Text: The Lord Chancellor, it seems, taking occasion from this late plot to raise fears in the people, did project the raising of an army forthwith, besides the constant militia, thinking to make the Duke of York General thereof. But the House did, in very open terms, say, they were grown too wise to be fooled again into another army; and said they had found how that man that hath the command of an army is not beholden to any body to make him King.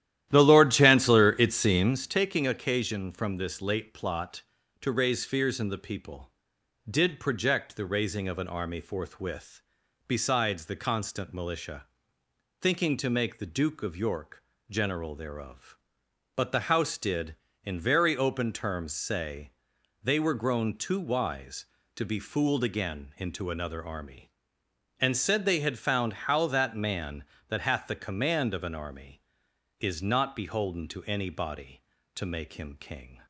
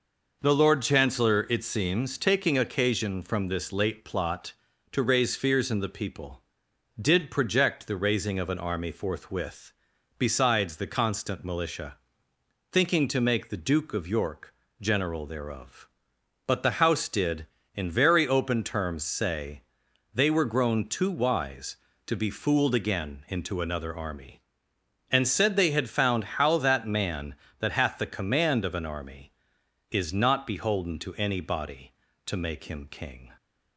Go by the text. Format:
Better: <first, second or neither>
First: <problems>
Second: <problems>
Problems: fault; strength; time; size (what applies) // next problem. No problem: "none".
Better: second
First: starts louder than the rest; strong; until 2.1 s; 12.5 dB // pauses between "York" and "General"; slight; at 14.4 s; 0.26 s long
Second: pauses between "York" and "General"; slight; at 14.5 s; 0.26 s long